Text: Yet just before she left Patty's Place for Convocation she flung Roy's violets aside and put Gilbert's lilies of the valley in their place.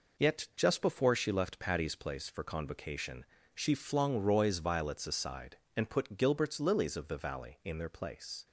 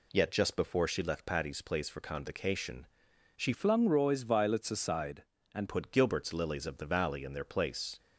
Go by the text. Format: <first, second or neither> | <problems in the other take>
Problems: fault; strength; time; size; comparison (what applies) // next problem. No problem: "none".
first | pauses between "Convocation" and "she"; noticeable; at 2.8 s; 0.52 s long; slight in the first // changes voice from "flung" to "and"; from 3.5 to 5.6 s; 2.1 s long